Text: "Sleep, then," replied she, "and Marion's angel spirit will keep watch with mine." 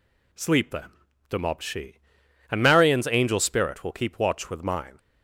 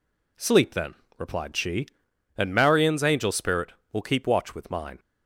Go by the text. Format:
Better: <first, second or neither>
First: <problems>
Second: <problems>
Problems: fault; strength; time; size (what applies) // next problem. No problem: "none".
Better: second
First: says "demobbed" for "replied"; at 1.2 s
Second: none